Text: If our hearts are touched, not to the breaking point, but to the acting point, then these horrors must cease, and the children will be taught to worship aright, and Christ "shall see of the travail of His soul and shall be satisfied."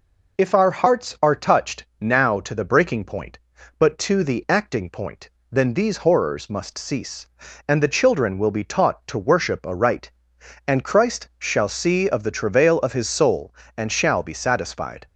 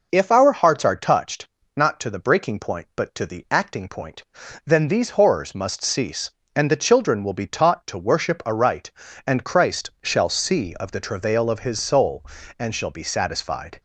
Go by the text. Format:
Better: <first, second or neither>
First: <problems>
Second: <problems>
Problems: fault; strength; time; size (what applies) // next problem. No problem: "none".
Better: second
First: says "now" for "not"; at 2.0 s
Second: none